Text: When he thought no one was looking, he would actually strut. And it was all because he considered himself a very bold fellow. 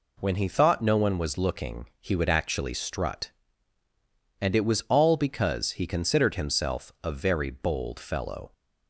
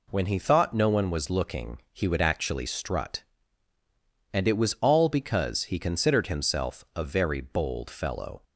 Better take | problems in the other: neither | none

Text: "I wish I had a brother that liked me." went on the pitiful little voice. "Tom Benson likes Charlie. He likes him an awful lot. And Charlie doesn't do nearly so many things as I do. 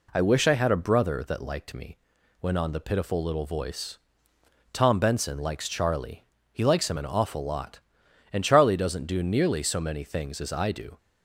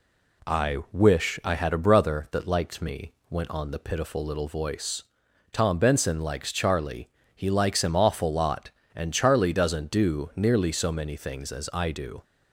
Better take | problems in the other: first | skips "an"; at 7.9 s

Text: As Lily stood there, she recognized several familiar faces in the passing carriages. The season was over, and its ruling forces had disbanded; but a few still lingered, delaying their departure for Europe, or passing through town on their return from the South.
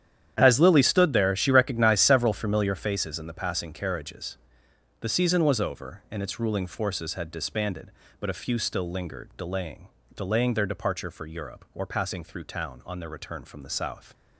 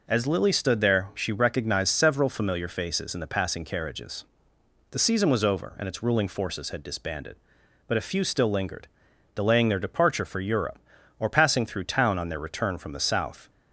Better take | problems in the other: second | starts louder than the rest; strong; until 1.3 s; 10 dB // says "delaying" twice; at 10.1 s

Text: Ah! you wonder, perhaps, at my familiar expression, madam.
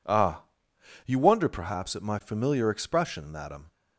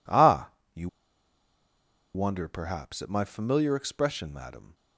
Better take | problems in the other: first | pauses between "you" and "wonder"; strong; at 0.8 s; 1.2 s long

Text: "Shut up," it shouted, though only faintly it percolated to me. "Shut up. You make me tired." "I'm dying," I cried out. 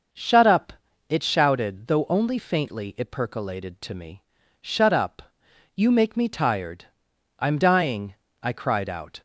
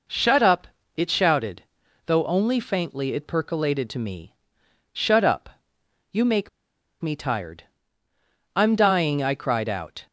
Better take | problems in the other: first | pauses between "make" and "me"; noticeable; at 6.4 s; 0.51 s long

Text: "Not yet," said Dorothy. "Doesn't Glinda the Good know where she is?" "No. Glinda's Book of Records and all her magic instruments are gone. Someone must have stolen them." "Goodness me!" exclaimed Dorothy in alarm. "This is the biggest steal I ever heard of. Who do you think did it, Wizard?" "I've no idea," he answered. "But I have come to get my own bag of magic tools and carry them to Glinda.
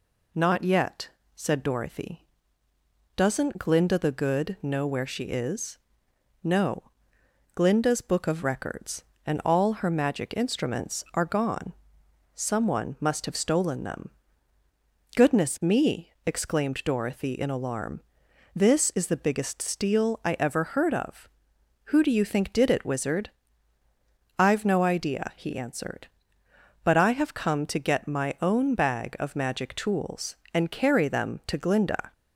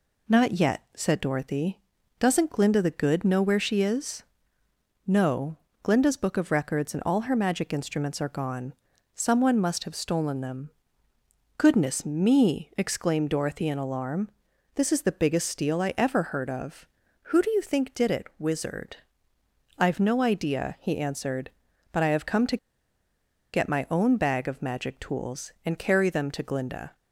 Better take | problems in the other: first | pauses between "to" and "get"; noticeable; at 22.5 s; 0.96 s long

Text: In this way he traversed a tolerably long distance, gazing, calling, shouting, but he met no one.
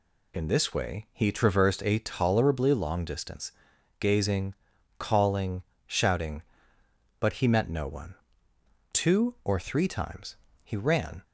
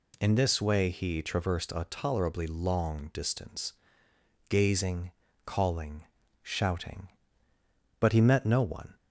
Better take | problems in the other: second | goes on to say "Two or three times he ran"; strong; from 8.9 s on; 2.3 s long

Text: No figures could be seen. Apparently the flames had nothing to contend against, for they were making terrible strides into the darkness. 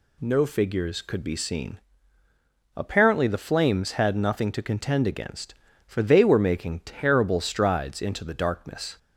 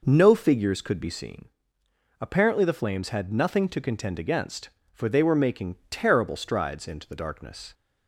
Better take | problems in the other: neither | none

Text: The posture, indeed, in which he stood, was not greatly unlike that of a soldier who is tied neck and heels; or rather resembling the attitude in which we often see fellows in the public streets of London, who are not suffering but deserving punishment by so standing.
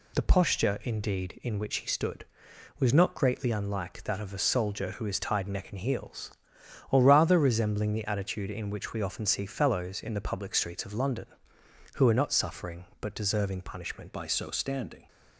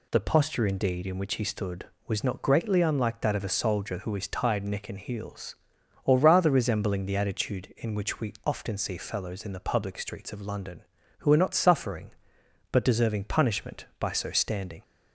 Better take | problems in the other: second | changes voice at "by"; from 14.1 s on; 0.9 s long

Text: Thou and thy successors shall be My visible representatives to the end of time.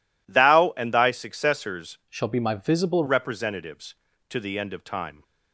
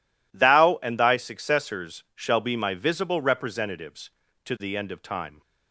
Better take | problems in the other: second | changes voice from "shall" to "visible"; from 2.0 to 3.0 s; 1.0 s long

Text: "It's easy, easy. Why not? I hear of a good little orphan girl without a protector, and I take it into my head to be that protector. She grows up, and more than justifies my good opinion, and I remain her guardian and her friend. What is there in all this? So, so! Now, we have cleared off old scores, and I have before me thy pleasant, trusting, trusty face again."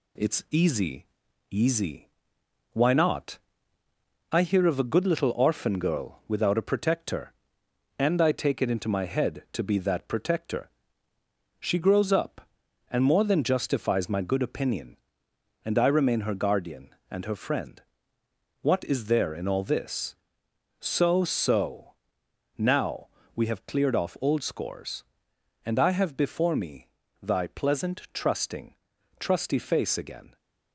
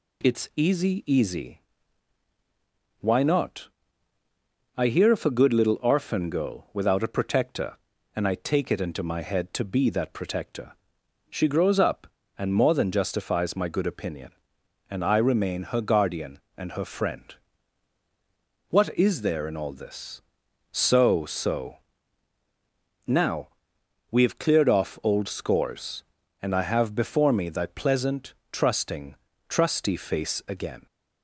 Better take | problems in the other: second | gets quieter; slight; throughout; 2.5 dB // pauses between "me" and "thy"; slight; at 26.8 s; 0.34 s long

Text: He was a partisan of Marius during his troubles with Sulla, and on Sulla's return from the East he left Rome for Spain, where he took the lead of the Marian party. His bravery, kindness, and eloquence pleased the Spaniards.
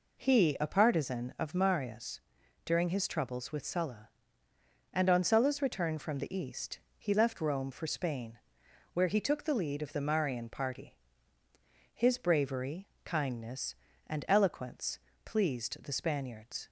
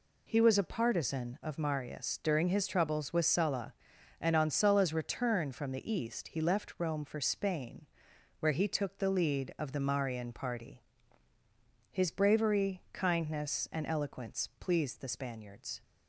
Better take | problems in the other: second | skips "was"; at 0.5 s // pauses between "Marius" and "during"; noticeable; at 2.1 s; 0.46 s long // pauses between "East" and "he"; slight; at 6.7 s; 0.18 s long // pauses between "eloquence" and "pleased"; slight; at 14.9 s; 0.24 s long

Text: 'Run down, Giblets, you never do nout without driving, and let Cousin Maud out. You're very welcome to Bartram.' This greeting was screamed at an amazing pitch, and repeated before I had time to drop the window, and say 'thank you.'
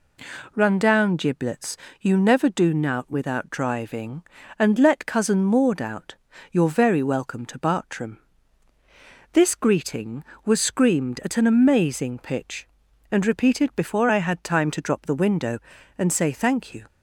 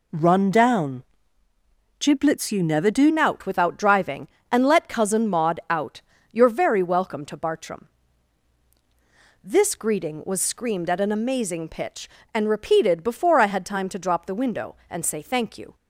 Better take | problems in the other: first | changes voice at "nout"; from 3.0 s on; 12.7 s long

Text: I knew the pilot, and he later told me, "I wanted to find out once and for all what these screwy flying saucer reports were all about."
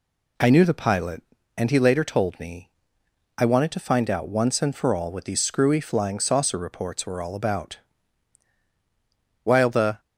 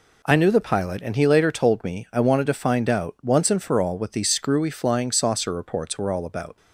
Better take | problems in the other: second | goes on to say "While the"; from 9.4 s on; 0.56 s long

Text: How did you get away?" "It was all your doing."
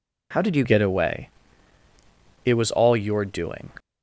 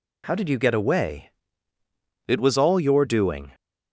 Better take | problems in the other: second | changes voice at "get"; from 0.6 s on; 3.1 s long

